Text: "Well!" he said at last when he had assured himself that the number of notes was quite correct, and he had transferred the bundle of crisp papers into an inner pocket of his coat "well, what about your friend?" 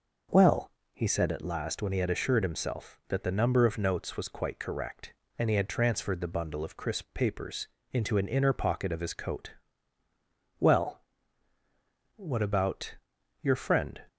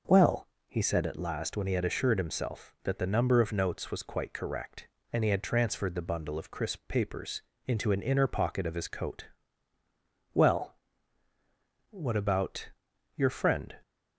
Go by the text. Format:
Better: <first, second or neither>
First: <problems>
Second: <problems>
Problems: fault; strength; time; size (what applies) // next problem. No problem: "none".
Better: neither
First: pauses between "papers" and "into"; slight; at 7.6 s; 0.24 s long // pauses between "coat" and "well"; at 9.5 s; 1.0 s long // pauses between "about" and "your"; noticeable; at 12.9 s; 0.48 s long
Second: pauses between "papers" and "into"; slight; at 7.4 s; 0.24 s long // pauses between "coat" and "well"; at 9.2 s; 1.0 s long // pauses between "about" and "your"; noticeable; at 12.6 s; 0.48 s long